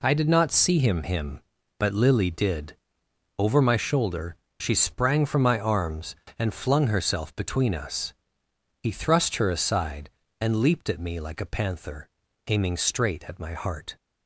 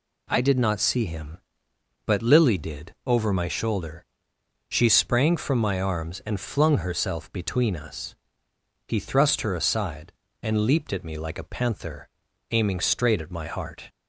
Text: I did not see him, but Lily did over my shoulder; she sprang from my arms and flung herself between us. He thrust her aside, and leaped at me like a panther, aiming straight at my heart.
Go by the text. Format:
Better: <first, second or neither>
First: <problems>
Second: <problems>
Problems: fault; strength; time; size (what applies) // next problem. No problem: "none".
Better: second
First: says "him" twice; at 1.0 s // pauses between "did" and "over"; noticeable; at 2.7 s; 0.62 s long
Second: none